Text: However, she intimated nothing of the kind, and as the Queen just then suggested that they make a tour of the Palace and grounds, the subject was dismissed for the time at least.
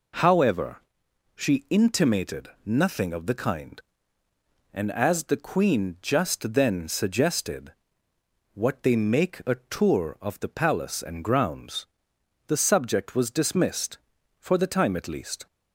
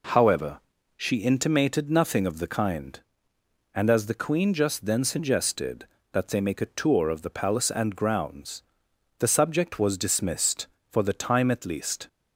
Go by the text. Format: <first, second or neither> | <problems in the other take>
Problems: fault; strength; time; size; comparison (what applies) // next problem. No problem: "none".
second | pauses between "intimated" and "nothing"; slight; at 2.4 s; 0.18 s long // says "what" for "that"; at 8.5 s